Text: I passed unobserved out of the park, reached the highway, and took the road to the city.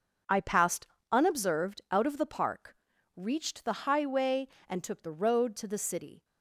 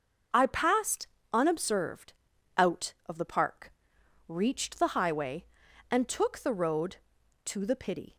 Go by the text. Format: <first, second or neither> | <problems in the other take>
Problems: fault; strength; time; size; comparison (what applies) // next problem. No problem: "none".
first | starts louder than the rest; noticeable; until 1.6 s; 6 dB; also in the first // pauses between "passed" and "unobserved"; slight; at 1.0 s; 0.26 s long; slight in the first // pauses between "unobserved" and "out"; at 2.1 s; 0.42 s long // says "pity" for "city"; at 7.7 s